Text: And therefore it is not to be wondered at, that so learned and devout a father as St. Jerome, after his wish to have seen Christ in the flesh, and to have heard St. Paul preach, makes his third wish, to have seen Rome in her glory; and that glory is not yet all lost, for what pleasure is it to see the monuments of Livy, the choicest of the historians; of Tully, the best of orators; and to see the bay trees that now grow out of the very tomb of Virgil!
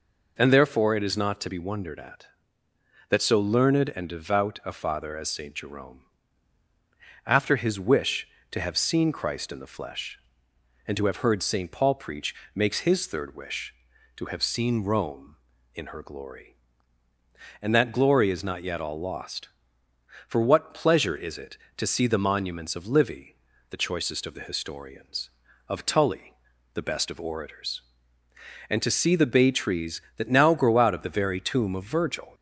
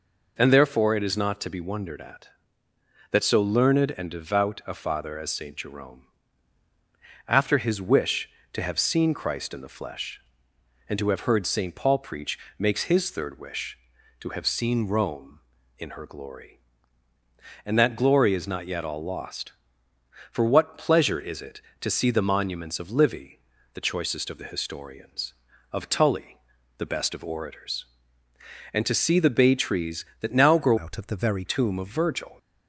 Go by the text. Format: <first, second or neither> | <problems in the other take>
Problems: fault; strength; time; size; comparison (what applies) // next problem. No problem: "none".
first | changes voice from "out" to "very"; from 30.7 to 31.4 s; 0.7 s long